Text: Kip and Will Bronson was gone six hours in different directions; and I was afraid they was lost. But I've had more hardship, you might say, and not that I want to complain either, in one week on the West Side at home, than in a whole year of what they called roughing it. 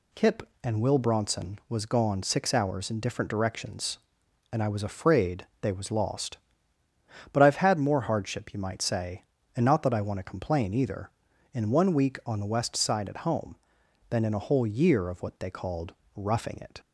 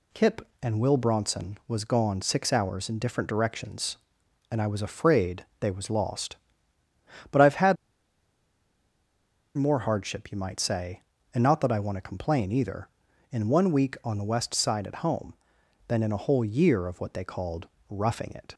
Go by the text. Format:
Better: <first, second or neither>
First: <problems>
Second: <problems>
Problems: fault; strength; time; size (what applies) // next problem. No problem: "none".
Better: first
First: pauses between "afraid" and "they"; slight; at 5.4 s; 0.16 s long // pauses between "called" and "roughing"; slight; at 15.9 s; 0.24 s long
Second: pauses between "afraid" and "they"; slight; at 5.4 s; 0.16 s long // pauses between "had" and "more"; strong; at 7.7 s; 1.8 s long // pauses between "called" and "roughing"; slight; at 17.6 s; 0.24 s long